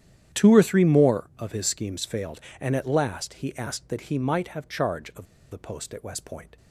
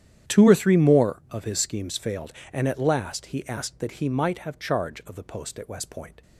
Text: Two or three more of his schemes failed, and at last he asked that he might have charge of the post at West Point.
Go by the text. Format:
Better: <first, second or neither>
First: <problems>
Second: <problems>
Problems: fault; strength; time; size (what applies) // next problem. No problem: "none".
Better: second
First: starts louder than the rest; strong; until 1.4 s; 10.5 dB // pauses between "of" and "the"; slight; at 5.2 s; 0.26 s long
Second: starts louder than the rest; strong; until 1.3 s; 10 dB